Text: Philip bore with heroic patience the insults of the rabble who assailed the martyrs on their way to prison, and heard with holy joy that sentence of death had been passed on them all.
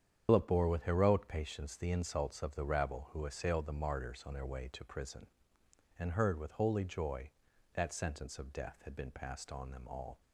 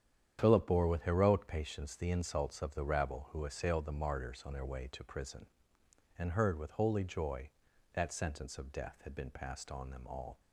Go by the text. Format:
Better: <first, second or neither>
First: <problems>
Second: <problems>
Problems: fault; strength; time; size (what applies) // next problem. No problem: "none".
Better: second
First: loses the start of "Philip"; at 0.2 s; 95 ms // starts louder than the rest; strong; until 1.2 s; 8.5 dB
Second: starts louder than the rest; strong; until 1.4 s; 9 dB